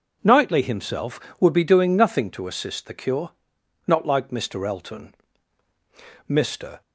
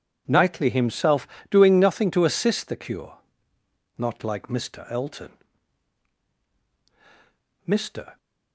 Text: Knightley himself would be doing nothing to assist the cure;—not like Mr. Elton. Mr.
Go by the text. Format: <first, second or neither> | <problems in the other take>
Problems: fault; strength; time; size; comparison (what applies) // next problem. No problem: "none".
first | skips "would be"; at 1.3 s